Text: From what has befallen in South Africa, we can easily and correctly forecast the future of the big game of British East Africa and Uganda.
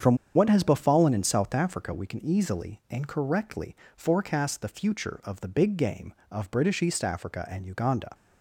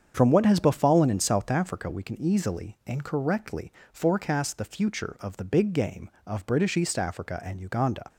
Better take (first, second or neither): second